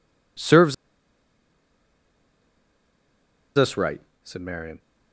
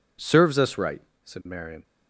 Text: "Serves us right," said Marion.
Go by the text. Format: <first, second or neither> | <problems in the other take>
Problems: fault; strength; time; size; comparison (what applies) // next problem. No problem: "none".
second | pauses between "Serves" and "us"; strong; at 0.7 s; 2.8 s long